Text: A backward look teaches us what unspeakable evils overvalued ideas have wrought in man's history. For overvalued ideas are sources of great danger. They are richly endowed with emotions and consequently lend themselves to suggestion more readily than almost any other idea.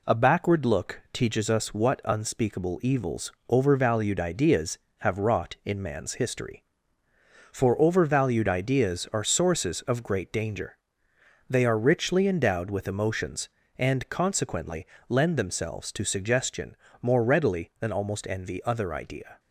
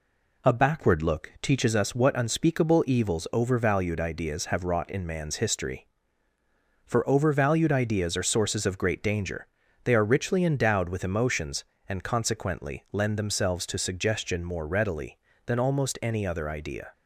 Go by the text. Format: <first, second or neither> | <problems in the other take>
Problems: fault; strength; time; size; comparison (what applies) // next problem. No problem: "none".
second | pauses between "evils" and "overvalued"; slight; at 3.3 s; 0.16 s long // pauses between "consequently" and "lend"; slight; at 14.8 s; 0.22 s long // pauses between "suggestion" and "more"; slight; at 16.7 s; 0.26 s long // says "envy" for "any"; at 18.2 s